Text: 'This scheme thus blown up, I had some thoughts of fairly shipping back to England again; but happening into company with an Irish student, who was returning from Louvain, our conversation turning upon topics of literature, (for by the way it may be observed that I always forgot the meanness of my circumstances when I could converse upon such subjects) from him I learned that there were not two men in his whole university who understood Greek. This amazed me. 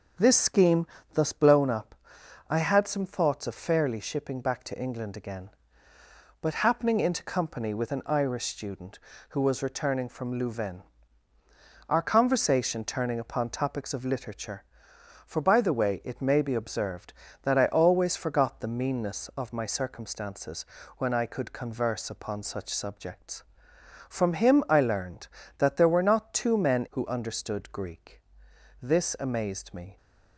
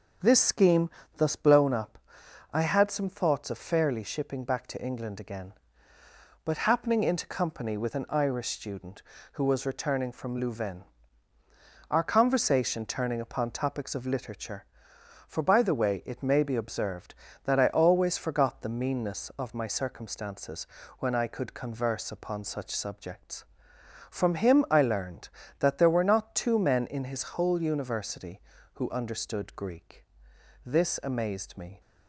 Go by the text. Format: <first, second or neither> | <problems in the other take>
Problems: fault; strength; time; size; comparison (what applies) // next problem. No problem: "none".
second | pauses between "scheme" and "thus"; slight; at 0.8 s; 0.26 s long; slight in the second // pauses between "circumstances" and "when"; slight; at 20.6 s; 0.32 s long; slight in the second // skips "in his whole university"; at 26.9 s